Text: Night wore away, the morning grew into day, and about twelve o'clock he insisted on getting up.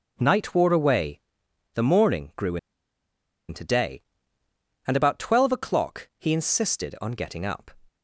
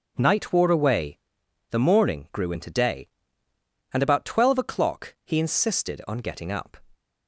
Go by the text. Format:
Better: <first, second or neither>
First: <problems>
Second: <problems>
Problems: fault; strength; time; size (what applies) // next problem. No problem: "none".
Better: second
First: pauses between "grew" and "into"; noticeable; at 2.5 s; 0.92 s long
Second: none